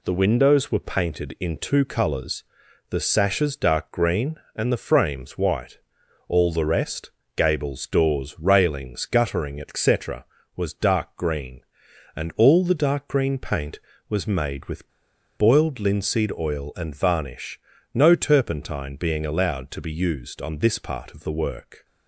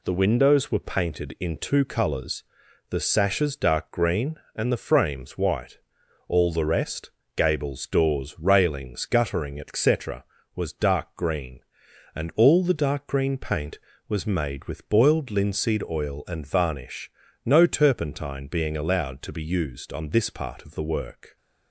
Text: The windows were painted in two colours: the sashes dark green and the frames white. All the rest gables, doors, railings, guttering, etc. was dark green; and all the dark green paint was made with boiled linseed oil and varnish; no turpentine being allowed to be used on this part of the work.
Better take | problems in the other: second | pauses between "rest" and "gables"; slight; at 7.1 s; 0.26 s long; slight in the second // pauses between "with" and "boiled"; noticeable; at 14.8 s; 0.48 s long

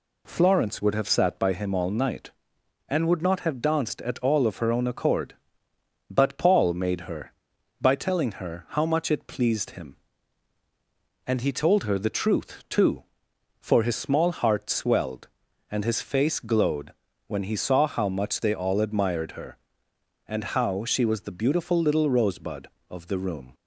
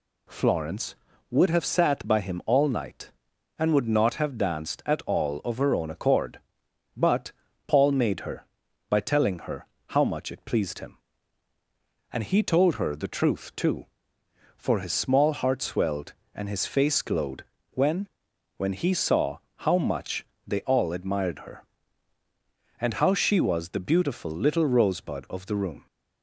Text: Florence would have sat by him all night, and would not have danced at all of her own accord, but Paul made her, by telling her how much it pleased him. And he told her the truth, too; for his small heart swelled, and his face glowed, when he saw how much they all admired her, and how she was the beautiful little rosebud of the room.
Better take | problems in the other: first | pauses between "but" and "Paul"; slight; at 7.3 s; 0.34 s long // pauses between "her" and "how"; slight; at 9.6 s; 0.22 s long // says "when" twice; at 18.5 s // pauses between "saw" and "how"; slight; at 19.3 s; 0.18 s long // pauses between "much" and "they"; slight; at 20.2 s; 0.20 s long

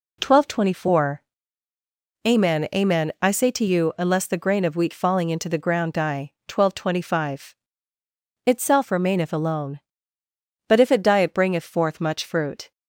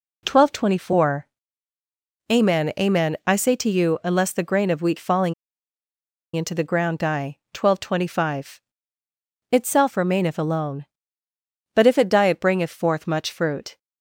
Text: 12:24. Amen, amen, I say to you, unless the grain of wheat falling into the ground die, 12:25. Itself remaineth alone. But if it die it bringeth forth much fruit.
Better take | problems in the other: first | pauses between "falling" and "into"; at 5.3 s; 1.0 s long

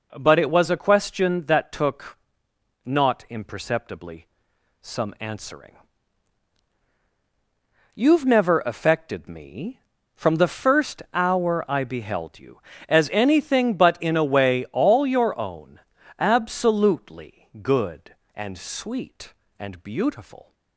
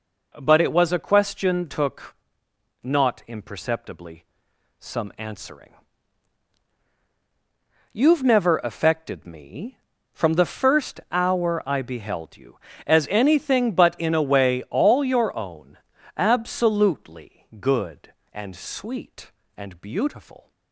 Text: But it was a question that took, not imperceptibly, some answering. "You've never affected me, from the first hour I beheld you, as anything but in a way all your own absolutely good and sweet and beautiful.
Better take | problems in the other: first | skips "that"; at 1.6 s // pauses between "own" and "absolutely"; at 15.7 s; 0.38 s long; also in the first

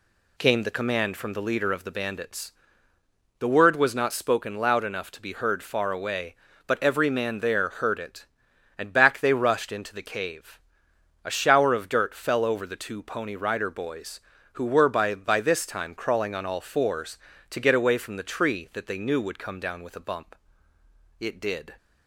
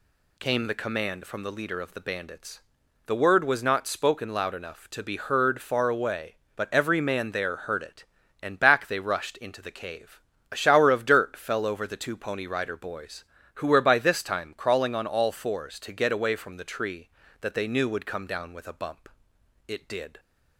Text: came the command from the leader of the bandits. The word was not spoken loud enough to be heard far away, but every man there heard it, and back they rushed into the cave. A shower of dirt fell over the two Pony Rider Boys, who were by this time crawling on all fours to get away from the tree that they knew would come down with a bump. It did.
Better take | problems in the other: second | says "by" twice; at 15.1 s

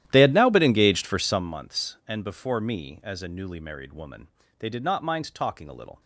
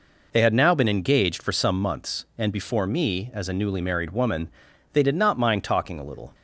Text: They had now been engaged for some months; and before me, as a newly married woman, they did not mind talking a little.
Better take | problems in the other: second | starts louder than the rest; strong; until 1.5 s; 12.5 dB

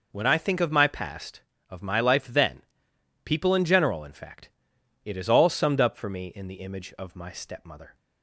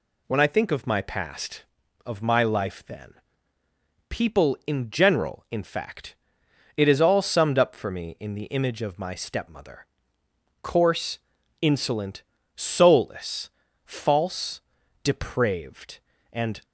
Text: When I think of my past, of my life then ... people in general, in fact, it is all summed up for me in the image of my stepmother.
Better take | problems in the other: first | goes on to say "Coarse insolent soulless false depraved and"; strong; from 10.6 s on; 6.0 s long

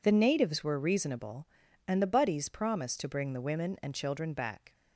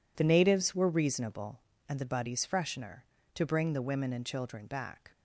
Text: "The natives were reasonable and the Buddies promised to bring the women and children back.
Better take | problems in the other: first | says "freshener" for "promised"; at 2.4 s

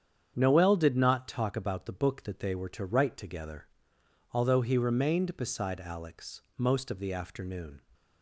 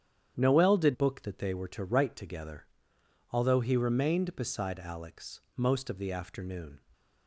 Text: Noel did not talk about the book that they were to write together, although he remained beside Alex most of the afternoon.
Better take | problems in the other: first | starts louder than the rest; strong; until 1.3 s; 9 dB; strong in the first // skips "not talk about the"; at 0.9 s // pauses between "Alex" and "most"; slight; at 5.4 s; 0.16 s long; slight in the first

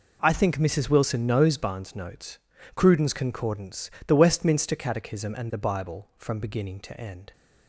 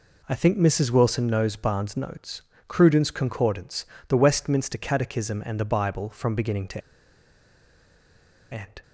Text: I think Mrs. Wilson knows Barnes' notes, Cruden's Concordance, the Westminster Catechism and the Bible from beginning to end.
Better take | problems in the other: first | pauses between "to" and "end"; strong; at 6.8 s; 1.7 s long

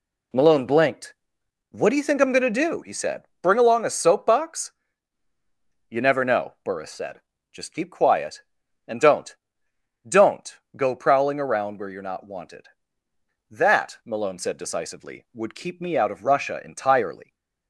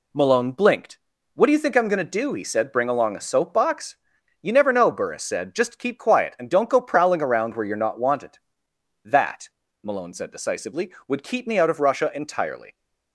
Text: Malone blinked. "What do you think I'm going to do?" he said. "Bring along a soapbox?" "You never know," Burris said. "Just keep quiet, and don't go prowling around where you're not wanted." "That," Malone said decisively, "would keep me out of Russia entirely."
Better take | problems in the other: second | says "don't" twice; at 10.0 s

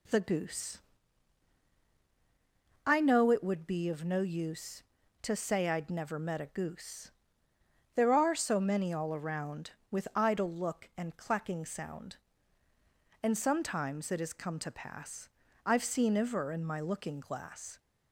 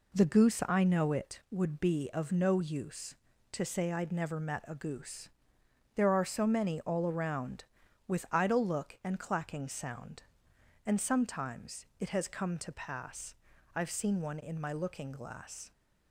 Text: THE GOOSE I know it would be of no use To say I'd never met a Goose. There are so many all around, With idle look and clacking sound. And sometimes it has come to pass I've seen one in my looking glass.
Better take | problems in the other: second | pauses between "GOOSE" and "I"; strong; at 0.7 s; 2.0 s long // pauses between "pass" and "I've"; slight; at 15.2 s; 0.34 s long; also in the second // says "iver" for "one"; at 16.1 s

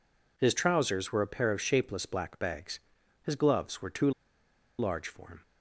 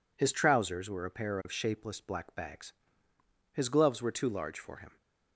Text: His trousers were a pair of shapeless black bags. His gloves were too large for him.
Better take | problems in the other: second | pauses between "too" and "large"; noticeable; at 4.1 s; 0.68 s long

